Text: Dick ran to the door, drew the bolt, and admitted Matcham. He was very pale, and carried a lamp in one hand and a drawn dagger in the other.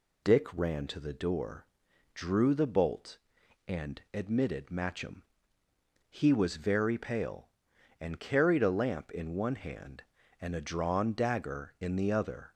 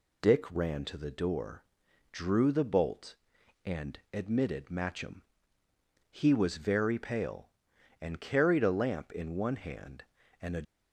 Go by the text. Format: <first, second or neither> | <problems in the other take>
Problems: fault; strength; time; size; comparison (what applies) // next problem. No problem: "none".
first | stops before "drawn dagger in the other"; at 10.6 s